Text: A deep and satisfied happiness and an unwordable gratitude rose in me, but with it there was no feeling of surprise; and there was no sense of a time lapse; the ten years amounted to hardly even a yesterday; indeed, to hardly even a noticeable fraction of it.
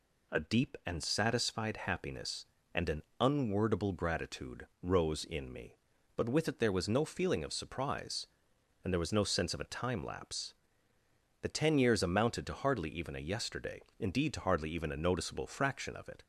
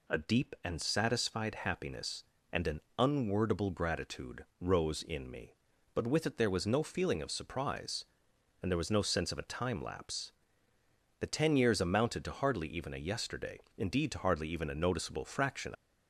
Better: first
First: pauses between "an" and "unwordable"; slight; at 3.0 s; 0.18 s long // pauses between "gratitude" and "rose"; slight; at 4.6 s; 0.16 s long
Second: pauses between "an" and "unwordable"; slight; at 2.7 s; 0.18 s long // pauses between "gratitude" and "rose"; slight; at 4.4 s; 0.16 s long // stops before "of it"; at 15.7 s

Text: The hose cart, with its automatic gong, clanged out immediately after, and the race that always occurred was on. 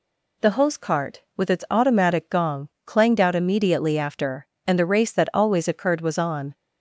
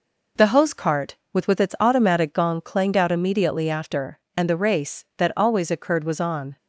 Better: first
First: none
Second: says "with" twice; at 1.4 s

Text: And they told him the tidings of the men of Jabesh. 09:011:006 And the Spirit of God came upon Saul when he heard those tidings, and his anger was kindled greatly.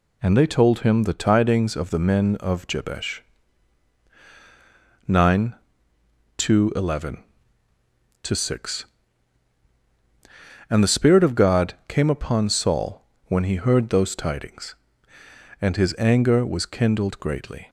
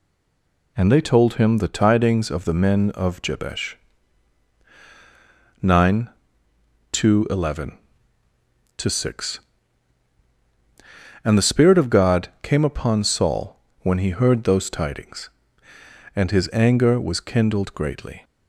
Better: first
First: pauses between "Saul" and "when"; slight; at 13.0 s; 0.22 s long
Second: stays silent before the first word; slight; until 0.7 s; 0.7 s long // pauses between "Saul" and "when"; slight; at 13.5 s; 0.22 s long

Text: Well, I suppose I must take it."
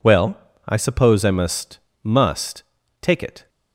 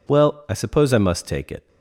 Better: second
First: says "must" twice; at 2.0 s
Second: none

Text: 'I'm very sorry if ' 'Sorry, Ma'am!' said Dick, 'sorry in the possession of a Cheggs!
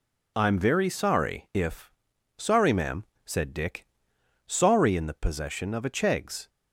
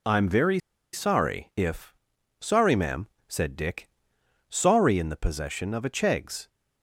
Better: first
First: none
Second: pauses between "very" and "sorry"; slight; at 0.5 s; 0.33 s long

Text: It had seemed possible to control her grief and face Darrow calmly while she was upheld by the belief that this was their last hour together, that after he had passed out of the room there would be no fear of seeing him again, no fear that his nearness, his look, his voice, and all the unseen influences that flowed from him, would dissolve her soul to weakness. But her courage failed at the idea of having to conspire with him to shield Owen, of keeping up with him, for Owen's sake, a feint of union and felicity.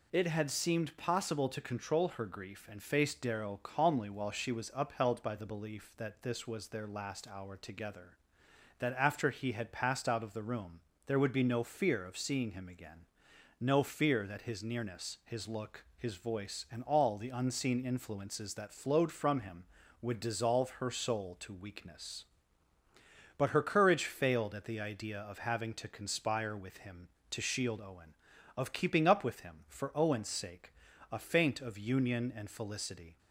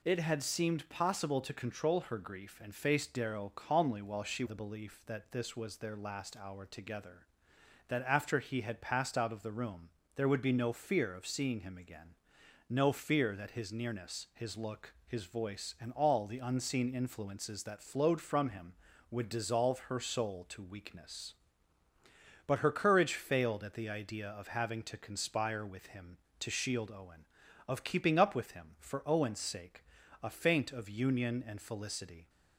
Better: first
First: pauses between "room" and "there"; slight; at 10.7 s; 0.26 s long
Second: skips "was upheld by"; at 4.4 s // pauses between "room" and "there"; slight; at 9.8 s; 0.26 s long

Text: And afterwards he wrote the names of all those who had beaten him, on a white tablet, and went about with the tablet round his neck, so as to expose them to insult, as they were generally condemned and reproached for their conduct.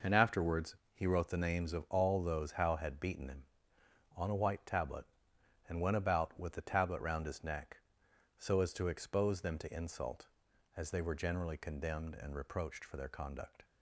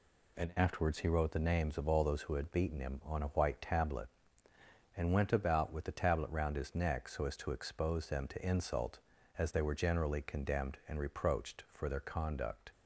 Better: second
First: pauses between "afterwards" and "he"; slight; at 0.7 s; 0.18 s long // says "how" for "who"; at 2.5 s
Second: none

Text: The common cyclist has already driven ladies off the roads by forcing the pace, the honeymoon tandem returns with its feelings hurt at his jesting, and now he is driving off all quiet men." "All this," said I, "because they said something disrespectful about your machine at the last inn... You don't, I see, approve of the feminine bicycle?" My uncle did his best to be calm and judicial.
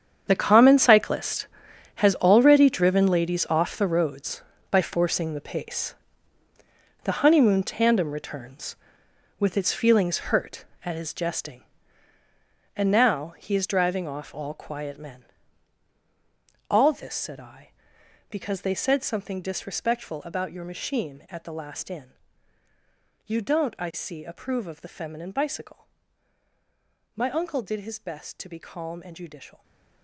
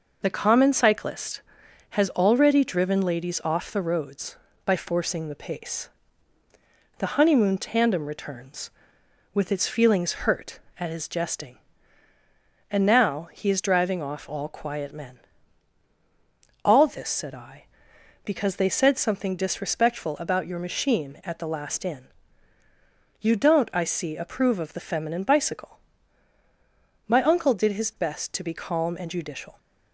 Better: second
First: gets quieter; strong; throughout; 15 dB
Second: none

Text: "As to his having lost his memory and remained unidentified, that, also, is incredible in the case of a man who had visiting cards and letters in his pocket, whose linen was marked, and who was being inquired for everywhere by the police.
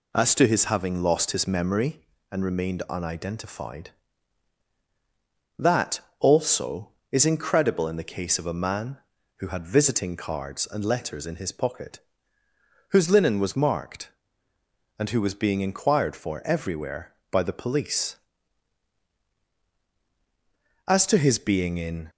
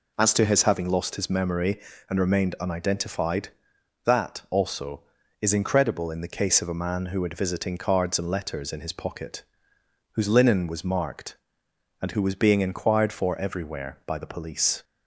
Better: second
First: goes on to say "As to his being in"; noticeable; from 20.8 s on; 1.2 s long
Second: none

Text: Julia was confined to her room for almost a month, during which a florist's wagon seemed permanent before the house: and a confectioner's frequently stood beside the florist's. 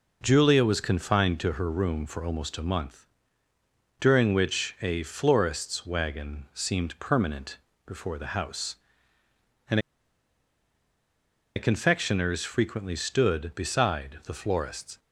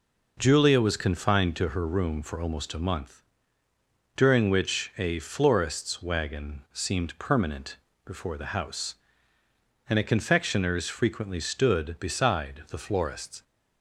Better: second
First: pauses between "permanent" and "before"; slight; at 7.5 s; 0.28 s long // pauses between "and" and "a"; strong; at 9.7 s; 1.7 s long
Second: pauses between "permanent" and "before"; slight; at 7.7 s; 0.28 s long

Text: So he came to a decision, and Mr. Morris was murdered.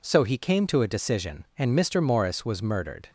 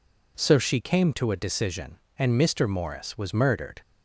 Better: first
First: none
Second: says "she" for "he"; at 0.5 s

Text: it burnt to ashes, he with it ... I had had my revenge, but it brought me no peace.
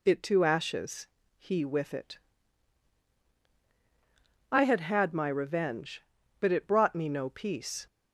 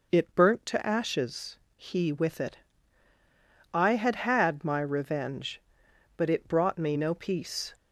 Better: second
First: skips "burnt"; at 0.2 s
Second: none

